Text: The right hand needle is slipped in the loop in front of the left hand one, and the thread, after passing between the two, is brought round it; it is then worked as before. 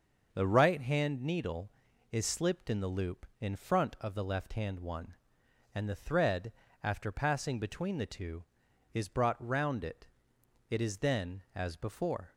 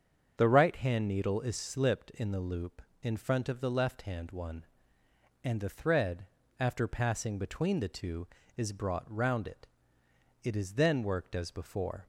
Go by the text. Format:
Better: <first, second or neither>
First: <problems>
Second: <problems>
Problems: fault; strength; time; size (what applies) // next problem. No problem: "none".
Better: second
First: starts louder than the rest; until 1.3 s; 6.5 dB // skips "worked"; at 11.4 s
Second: starts louder than the rest; until 1.4 s; 6.5 dB